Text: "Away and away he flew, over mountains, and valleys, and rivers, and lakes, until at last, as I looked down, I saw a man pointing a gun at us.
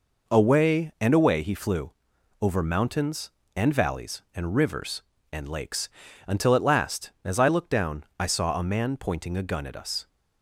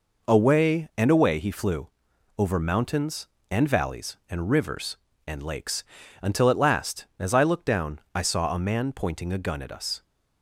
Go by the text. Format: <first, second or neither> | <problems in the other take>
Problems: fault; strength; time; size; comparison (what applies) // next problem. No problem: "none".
neither | none